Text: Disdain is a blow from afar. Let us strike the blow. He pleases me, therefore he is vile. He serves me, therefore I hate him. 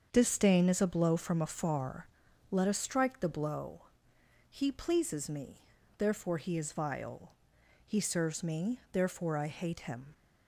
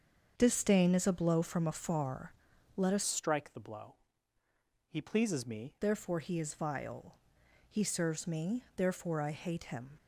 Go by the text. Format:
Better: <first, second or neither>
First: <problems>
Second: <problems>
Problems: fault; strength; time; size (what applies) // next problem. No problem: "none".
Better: first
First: starts louder than the rest; until 1.1 s; 7 dB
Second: starts louder than the rest; until 1.3 s; 7 dB // changes voice from "strike" to "me"; from 3.0 to 5.7 s; 2.7 s long